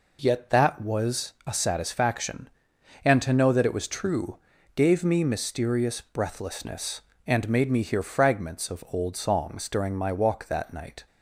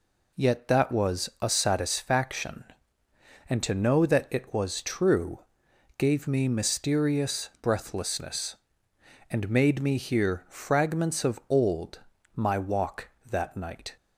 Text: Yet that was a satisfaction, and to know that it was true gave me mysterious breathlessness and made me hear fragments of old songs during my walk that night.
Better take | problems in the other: first | pauses between "true" and "gave"; noticeable; at 5.3 s; 0.60 s long; also in the first // skips "songs during"; at 12.1 s

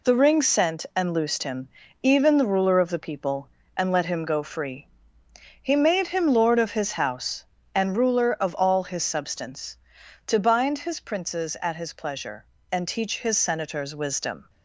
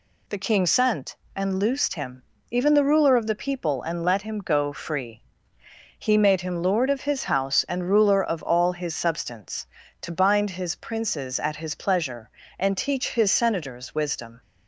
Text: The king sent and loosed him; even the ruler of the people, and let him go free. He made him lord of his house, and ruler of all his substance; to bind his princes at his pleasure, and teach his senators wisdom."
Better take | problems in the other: second | says "ring" for "king"; at 0.1 s

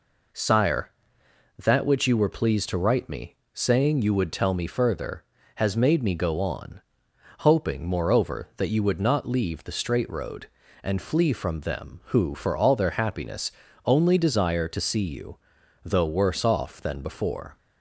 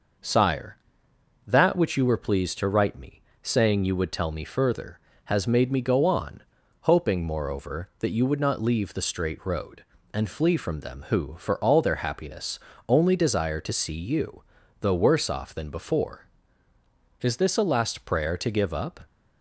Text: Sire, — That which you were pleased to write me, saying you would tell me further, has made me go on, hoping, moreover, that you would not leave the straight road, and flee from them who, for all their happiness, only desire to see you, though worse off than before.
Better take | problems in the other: first | goes on to say "Is this a last prayer to give up"; strong; from 17.2 s on; 1.8 s long

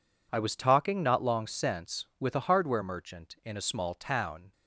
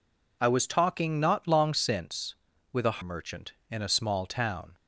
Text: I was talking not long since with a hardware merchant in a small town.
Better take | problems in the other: first | skips "hardware"; at 3.0 s

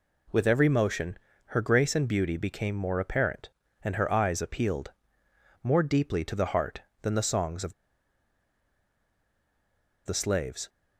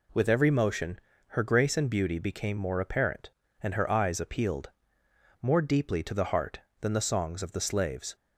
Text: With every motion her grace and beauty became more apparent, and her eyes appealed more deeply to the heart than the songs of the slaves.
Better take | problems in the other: second | pauses between "motion" and "her"; slight; at 1.1 s; 0.30 s long; slight in the second // pauses between "appealed" and "more"; noticeable; at 4.9 s; 0.72 s long; noticeable in the second // pauses between "of" and "the"; strong; at 7.7 s; 2.3 s long

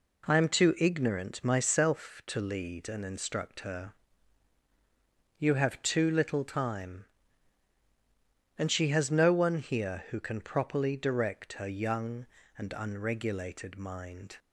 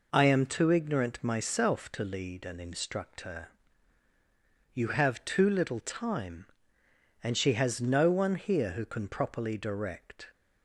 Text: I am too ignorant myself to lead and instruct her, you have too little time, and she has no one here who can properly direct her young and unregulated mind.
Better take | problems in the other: first | stops before "her young and unregulated mind"; at 10.3 s

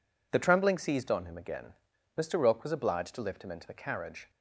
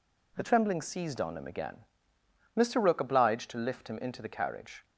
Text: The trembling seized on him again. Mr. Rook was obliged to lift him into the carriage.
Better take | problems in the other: first | skips "was"; at 2.9 s

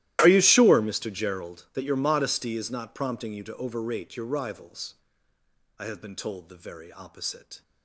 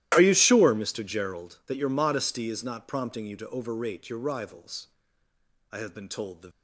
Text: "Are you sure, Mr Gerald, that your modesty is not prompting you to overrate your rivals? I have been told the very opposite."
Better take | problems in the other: first | starts louder than the rest; strong; until 1.1 s; 14 dB; strong in the first // stops before "very opposite"; at 6.5 s

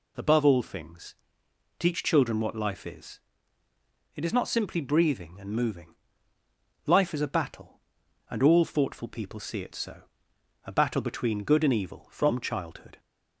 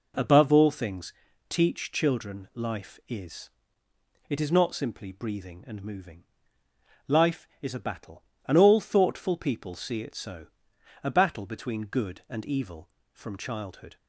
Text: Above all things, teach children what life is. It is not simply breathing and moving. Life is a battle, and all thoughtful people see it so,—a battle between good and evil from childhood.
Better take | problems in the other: first | skips "what"; at 2.5 s

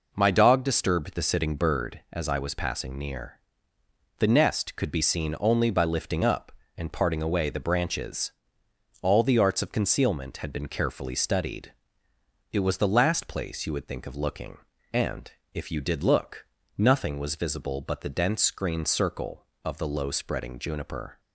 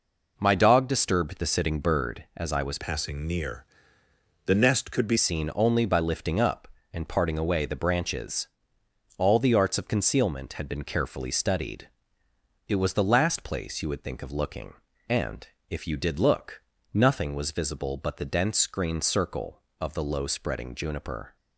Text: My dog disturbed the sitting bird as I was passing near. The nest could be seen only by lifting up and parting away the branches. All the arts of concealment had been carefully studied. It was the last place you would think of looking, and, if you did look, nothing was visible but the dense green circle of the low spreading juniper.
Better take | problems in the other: first | changes voice from "passing" to "be"; from 2.7 to 5.1 s; 2.4 s long

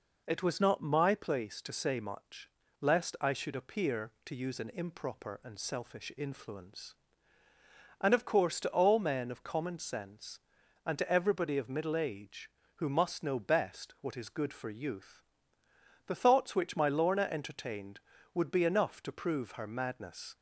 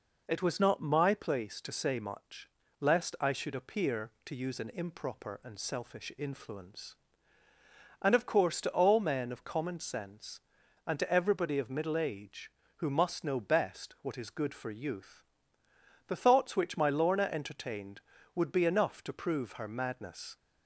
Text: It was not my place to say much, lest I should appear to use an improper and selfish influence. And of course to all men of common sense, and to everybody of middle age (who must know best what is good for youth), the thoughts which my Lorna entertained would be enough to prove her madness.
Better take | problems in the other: neither | none

